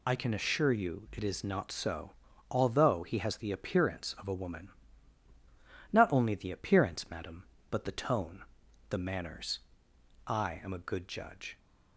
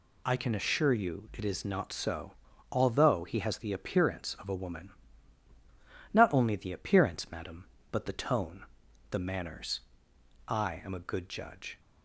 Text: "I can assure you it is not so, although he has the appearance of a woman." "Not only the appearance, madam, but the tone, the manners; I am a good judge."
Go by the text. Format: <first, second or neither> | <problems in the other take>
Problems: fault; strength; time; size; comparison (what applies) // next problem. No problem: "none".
second | loses the start of "I"; at 0.0 s; 25 ms